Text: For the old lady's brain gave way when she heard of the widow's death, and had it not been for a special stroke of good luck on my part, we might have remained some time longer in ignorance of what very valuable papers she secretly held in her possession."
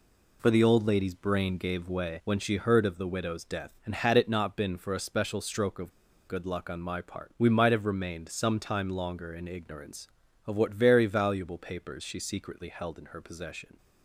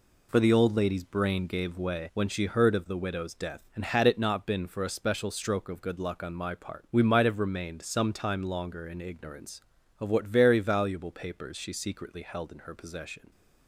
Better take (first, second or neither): second